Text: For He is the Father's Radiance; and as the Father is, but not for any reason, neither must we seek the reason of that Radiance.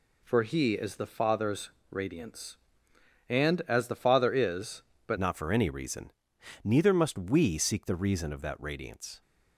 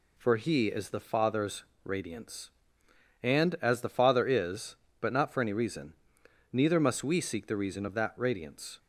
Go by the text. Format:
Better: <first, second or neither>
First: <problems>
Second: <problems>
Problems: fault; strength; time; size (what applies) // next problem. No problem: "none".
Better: second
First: pauses between "Father's" and "Radiance"; slight; at 1.7 s; 0.20 s long // changes voice at "not"; from 5.1 s on; 4.1 s long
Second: pauses between "Father's" and "Radiance"; slight; at 1.6 s; 0.20 s long